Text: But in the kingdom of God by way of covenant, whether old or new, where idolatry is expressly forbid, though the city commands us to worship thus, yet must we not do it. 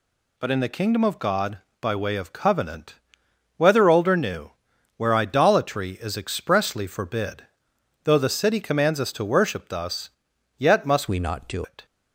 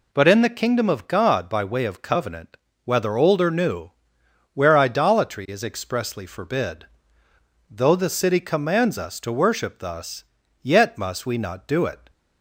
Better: second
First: changes voice from "we" to "do"; from 11.0 to 11.6 s; 0.6 s long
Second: none

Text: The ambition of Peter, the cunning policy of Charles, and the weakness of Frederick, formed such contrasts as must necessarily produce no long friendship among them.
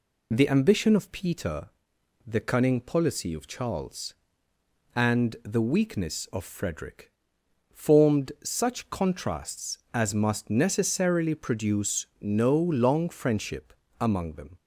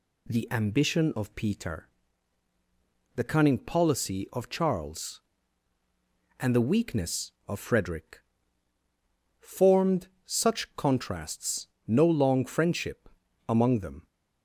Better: first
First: pauses between "friendship" and "among"; slight; at 13.7 s; 0.26 s long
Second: pauses between "formed" and "such"; slight; at 10.0 s; 0.18 s long // skips "as must necessarily produce"; at 11.7 s // pauses between "friendship" and "among"; at 13.0 s; 0.40 s long

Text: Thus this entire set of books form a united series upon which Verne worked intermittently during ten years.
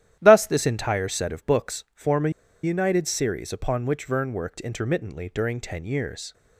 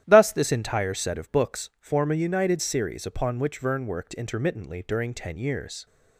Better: second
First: starts louder than the rest; strong; until 1.2 s; 11.5 dB // pauses between "a" and "united"; slight; at 2.2 s; 0.33 s long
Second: starts louder than the rest; strong; until 1.0 s; 11.5 dB

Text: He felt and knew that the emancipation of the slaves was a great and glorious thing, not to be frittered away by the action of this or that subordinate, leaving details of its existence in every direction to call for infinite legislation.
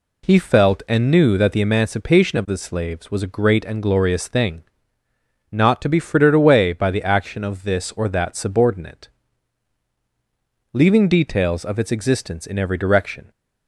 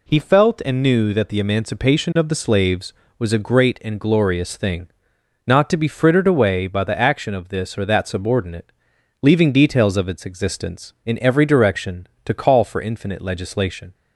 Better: second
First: stops before "to call for infinite legislation"; at 13.3 s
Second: none

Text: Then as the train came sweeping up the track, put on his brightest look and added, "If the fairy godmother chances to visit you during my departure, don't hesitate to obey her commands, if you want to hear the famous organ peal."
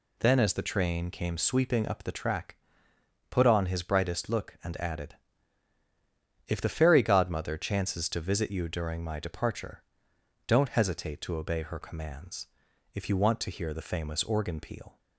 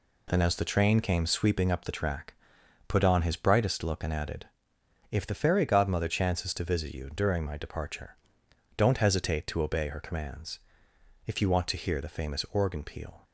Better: neither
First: none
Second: none

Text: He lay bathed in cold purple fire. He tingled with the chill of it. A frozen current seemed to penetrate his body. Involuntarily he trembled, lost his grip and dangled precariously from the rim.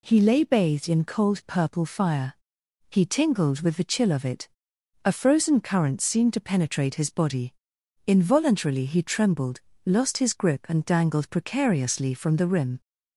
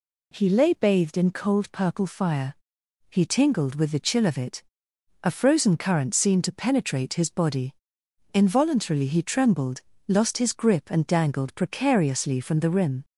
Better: neither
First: none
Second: none

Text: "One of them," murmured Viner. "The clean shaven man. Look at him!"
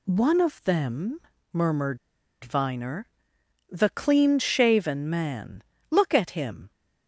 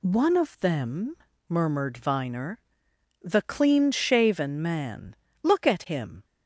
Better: second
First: pauses between "murmured" and "Viner"; at 1.9 s; 0.44 s long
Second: none

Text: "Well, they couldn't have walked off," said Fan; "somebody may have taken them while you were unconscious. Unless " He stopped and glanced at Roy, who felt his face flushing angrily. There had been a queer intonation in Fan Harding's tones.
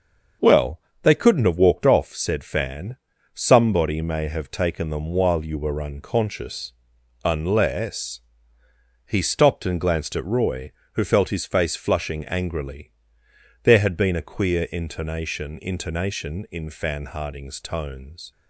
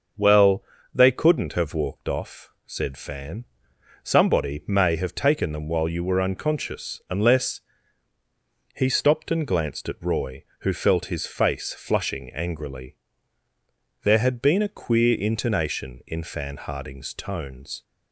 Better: second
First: starts louder than the rest; until 1.6 s; 6.5 dB // says "intonation" twice; at 15.6 s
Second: starts louder than the rest; until 1.4 s; 6.5 dB

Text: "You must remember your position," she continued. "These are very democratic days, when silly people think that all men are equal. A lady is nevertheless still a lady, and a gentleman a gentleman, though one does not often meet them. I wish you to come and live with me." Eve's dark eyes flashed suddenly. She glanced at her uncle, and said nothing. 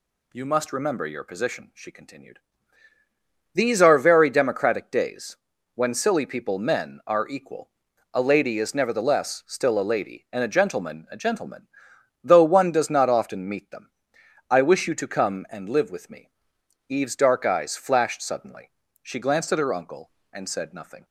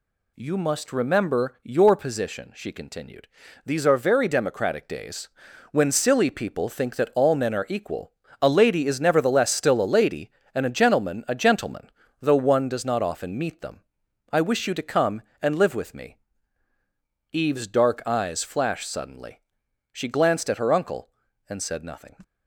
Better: second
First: skips "think that all"; at 6.5 s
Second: none

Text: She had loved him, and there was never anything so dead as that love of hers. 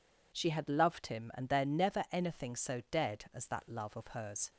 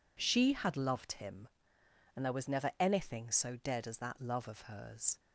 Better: second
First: skips "was"; at 1.6 s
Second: none

